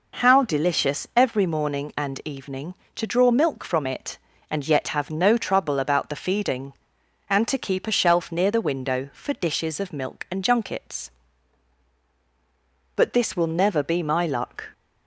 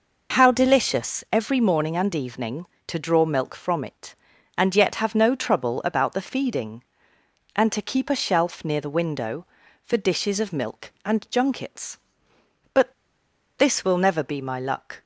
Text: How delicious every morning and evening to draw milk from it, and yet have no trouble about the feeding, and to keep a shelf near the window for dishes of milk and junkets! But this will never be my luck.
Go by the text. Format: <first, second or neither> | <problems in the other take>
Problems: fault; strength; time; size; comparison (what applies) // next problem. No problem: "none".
first | pauses between "But" and "this"; noticeable; at 12.9 s; 0.65 s long